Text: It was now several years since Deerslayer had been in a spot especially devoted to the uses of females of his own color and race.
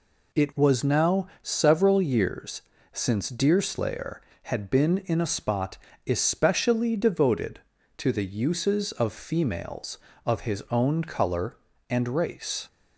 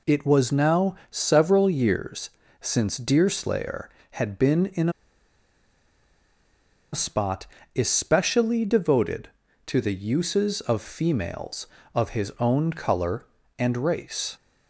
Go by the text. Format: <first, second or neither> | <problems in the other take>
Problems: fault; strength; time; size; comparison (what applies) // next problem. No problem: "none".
first | pauses between "now" and "several"; slight; at 0.9 s; 0.16 s long; slight in the first // pauses between "years" and "since"; slight; at 2.2 s; 0.30 s long; slight in the first // pauses between "in" and "a"; strong; at 4.8 s; 2.0 s long // pauses between "spot" and "especially"; slight; at 7.4 s; 0.30 s long; slight in the first